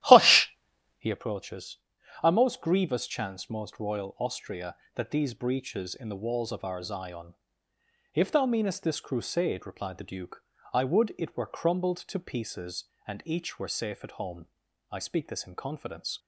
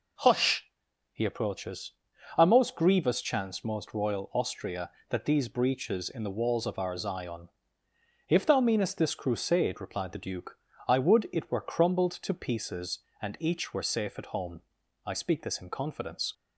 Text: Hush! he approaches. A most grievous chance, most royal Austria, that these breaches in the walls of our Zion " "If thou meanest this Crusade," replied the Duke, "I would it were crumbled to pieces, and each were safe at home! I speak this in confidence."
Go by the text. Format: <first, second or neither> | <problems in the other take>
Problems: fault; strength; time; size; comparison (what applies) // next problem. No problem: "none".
second | starts louder than the rest; strong; until 1.1 s; 13.5 dB